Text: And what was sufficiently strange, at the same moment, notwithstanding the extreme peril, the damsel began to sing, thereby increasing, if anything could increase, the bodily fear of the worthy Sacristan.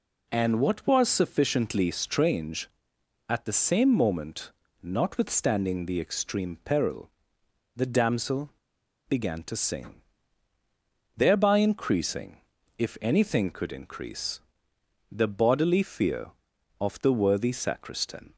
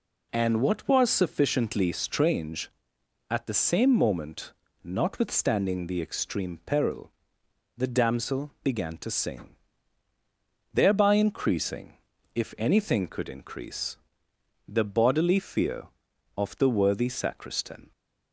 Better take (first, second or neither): second